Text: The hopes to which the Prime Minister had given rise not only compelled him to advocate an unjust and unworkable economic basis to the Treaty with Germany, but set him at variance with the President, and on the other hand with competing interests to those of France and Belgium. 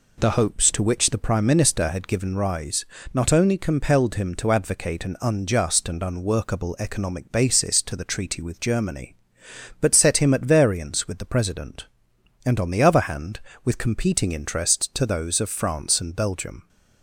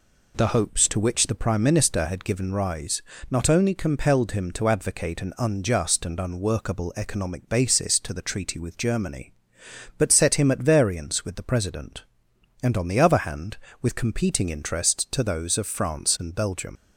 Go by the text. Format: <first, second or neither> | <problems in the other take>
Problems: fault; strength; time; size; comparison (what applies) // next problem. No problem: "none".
first | pauses between "rise" and "not"; slight; at 3.0 s; 0.28 s long; slight in the first // leaves "Belgium" unfinished; at 16.7 s; 125 ms